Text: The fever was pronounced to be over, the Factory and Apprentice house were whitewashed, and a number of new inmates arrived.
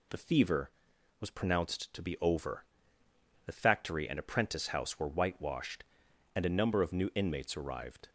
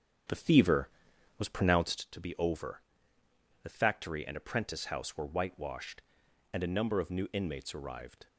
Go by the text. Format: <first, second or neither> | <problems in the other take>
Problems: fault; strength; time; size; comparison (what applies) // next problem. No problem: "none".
first | starts louder than the rest; strong; until 2.1 s; 8.5 dB